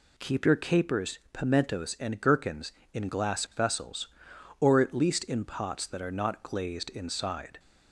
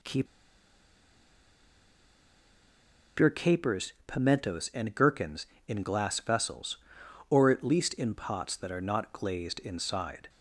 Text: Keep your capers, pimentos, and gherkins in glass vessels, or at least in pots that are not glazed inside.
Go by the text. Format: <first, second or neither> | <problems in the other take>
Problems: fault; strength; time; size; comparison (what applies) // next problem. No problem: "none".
first | pauses between "Keep" and "your"; strong; at 0.2 s; 2.9 s long